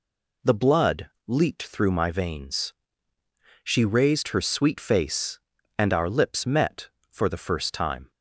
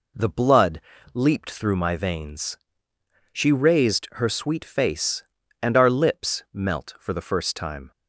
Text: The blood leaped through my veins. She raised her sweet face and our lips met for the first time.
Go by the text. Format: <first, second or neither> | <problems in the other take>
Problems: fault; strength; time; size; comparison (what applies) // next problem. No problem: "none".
first | pauses between "blood" and "leaped"; slight; at 0.8 s; 0.32 s long; slight in the first // says "melt" for "met"; at 6.5 s